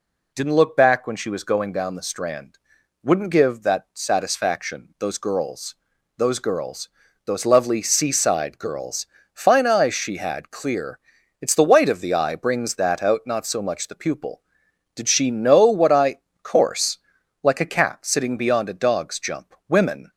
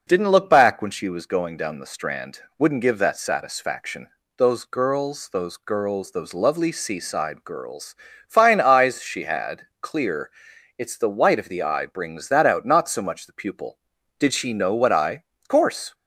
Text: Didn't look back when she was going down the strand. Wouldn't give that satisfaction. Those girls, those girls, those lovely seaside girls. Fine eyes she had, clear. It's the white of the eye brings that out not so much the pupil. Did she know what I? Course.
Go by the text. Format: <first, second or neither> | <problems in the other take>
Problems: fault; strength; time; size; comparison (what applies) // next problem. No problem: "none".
second | goes on to say "Like a cat sitting beyond a dog's jump Women"; strong; from 17.4 s on; 2.6 s long